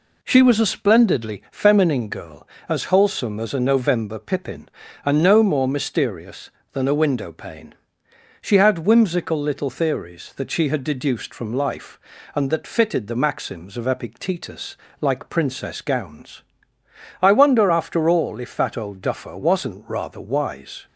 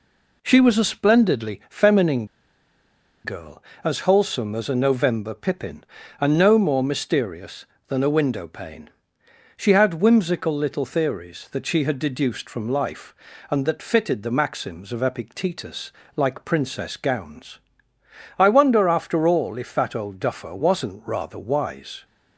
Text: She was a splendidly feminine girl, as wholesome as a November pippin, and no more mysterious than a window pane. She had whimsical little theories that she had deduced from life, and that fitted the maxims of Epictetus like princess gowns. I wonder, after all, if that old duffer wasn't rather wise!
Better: first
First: pauses between "Epictetus" and "like"; slight; at 14.7 s; 0.24 s long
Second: pauses between "feminine" and "girl"; at 2.2 s; 0.98 s long // pauses between "Epictetus" and "like"; slight; at 15.9 s; 0.24 s long

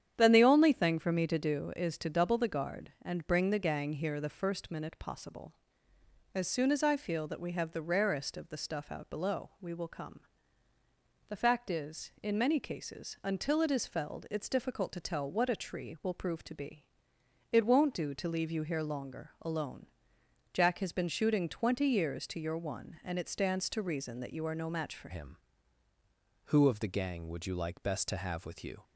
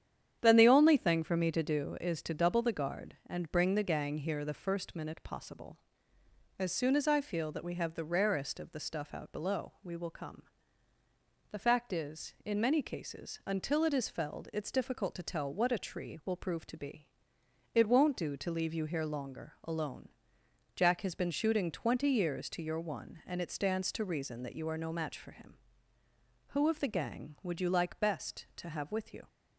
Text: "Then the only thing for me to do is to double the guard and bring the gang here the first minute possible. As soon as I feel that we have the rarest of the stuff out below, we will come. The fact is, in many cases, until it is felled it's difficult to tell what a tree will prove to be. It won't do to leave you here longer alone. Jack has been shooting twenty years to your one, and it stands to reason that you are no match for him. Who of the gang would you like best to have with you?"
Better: second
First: starts louder than the rest; strong; until 1.1 s; 9 dB // changes voice at "him"; from 25.1 s on; 3.7 s long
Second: starts louder than the rest; strong; until 1.4 s; 9 dB

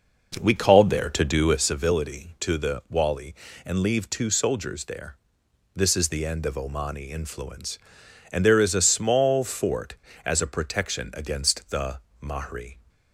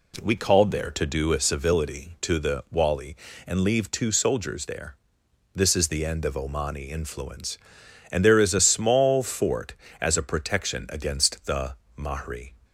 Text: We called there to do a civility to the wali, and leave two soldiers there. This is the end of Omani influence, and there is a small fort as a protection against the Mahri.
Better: second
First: starts louder than the rest; noticeable; until 1.7 s; 5.5 dB // pauses between "the" and "Mahri"; slight; at 11.9 s; 0.24 s long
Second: pauses between "the" and "Mahri"; slight; at 11.7 s; 0.24 s long

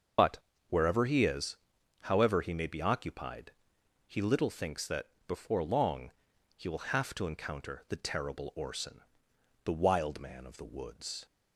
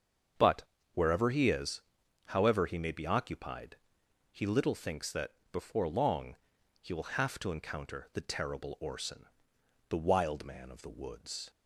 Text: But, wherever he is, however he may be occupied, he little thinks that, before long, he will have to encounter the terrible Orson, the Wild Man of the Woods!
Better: second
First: loses the start of "But"; at 0.1 s; 50 ms // starts louder than the rest; until 1.5 s; 6.5 dB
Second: starts louder than the rest; until 1.6 s; 7 dB

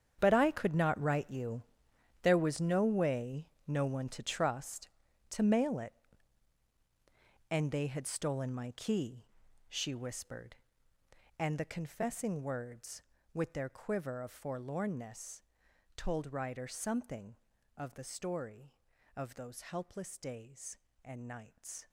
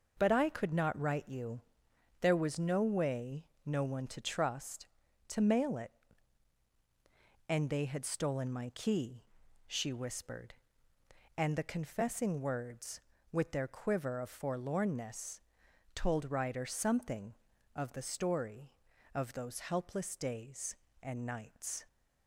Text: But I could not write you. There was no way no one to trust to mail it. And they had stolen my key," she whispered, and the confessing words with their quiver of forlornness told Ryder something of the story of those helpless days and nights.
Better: second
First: gets quieter; strong; throughout; 14.5 dB // pauses between "way" and "no"; slight; at 3.4 s; 0.20 s long // pauses between "forlornness" and "told"; noticeable; at 15.4 s; 0.52 s long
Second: pauses between "way" and "no"; slight; at 3.4 s; 0.20 s long // pauses between "forlornness" and "told"; noticeable; at 15.4 s; 0.52 s long

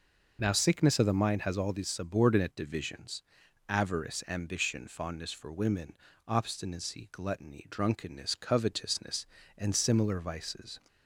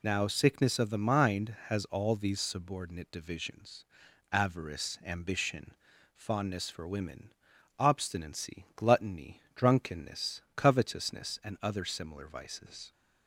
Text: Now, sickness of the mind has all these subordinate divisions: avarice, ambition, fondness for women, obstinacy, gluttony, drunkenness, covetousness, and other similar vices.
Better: second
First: skips "other"; at 9.7 s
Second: none

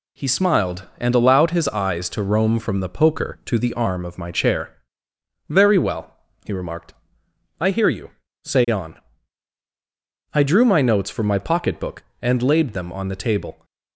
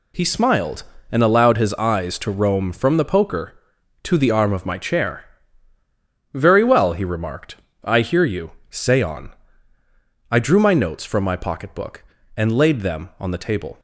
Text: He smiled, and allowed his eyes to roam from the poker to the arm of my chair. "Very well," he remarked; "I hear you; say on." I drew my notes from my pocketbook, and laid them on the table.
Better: neither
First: none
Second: none

